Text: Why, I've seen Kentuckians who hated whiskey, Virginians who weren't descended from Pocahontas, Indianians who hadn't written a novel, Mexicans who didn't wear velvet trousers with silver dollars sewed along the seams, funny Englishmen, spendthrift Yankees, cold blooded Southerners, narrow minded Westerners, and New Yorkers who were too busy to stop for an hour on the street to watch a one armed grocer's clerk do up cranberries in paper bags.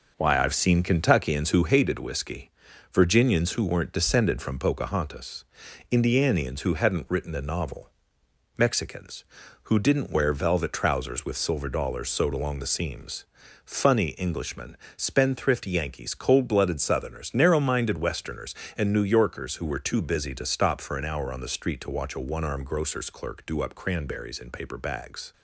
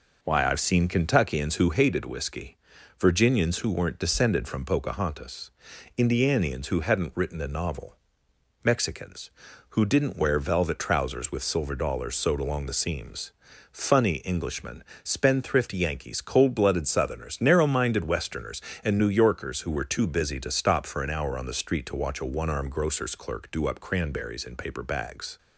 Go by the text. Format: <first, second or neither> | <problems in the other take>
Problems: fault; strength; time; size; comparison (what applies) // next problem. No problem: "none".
second | gets quieter; noticeable; throughout; 5 dB